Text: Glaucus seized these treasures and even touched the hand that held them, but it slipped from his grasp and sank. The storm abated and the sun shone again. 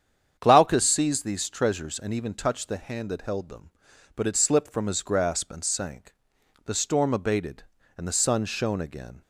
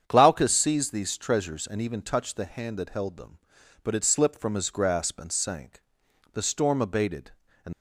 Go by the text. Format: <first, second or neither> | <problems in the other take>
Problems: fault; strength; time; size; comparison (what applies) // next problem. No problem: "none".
first | starts louder than the rest; strong; until 1.0 s; 8 dB; strong in the first // stops before "the sun shone again"; at 7.7 s